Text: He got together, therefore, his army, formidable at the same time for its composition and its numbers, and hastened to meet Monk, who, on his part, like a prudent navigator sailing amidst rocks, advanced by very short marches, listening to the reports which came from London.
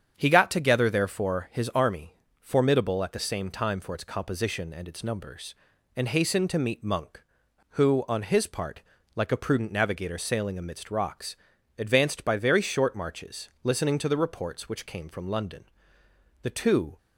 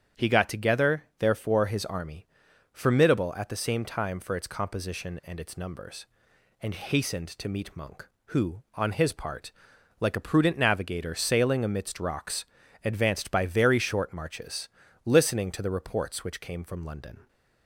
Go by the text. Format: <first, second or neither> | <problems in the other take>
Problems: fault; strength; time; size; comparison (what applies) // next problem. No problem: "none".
second | starts louder than the rest; strong; until 1.1 s; 8 dB; strong in the second // goes on to say "The two"; from 16.4 s on; 0.54 s long